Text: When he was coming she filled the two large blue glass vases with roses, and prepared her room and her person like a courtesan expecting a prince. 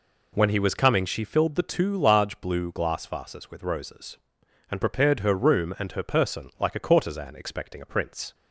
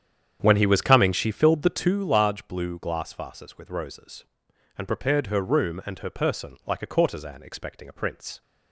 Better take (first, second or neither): first